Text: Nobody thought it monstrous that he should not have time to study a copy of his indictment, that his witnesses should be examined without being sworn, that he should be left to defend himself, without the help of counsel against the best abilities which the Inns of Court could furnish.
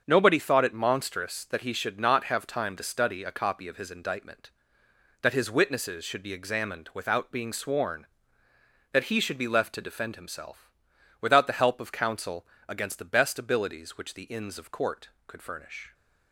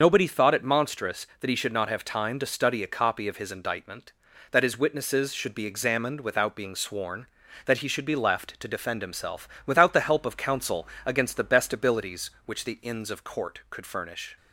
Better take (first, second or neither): first